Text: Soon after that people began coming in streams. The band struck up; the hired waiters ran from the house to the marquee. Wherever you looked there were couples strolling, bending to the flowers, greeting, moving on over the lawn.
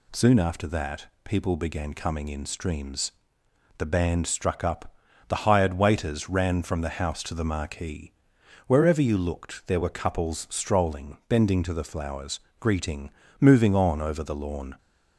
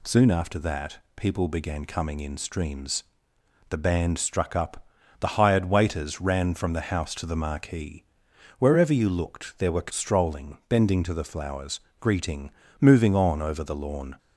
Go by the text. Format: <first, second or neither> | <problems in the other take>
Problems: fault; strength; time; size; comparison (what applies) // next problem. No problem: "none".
first | pauses between "that" and "people"; slight; at 0.9 s; 0.18 s long; slight in the first // skips "couples"; at 9.9 s